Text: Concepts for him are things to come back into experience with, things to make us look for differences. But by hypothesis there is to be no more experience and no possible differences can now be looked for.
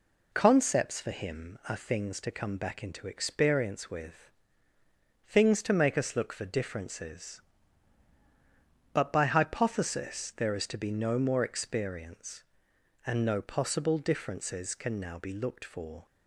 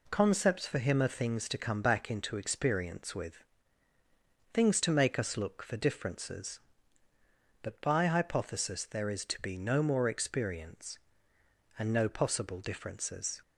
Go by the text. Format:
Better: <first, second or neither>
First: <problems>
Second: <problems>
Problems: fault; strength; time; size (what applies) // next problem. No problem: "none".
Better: first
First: none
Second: stops before "can now be looked for"; at 13.4 s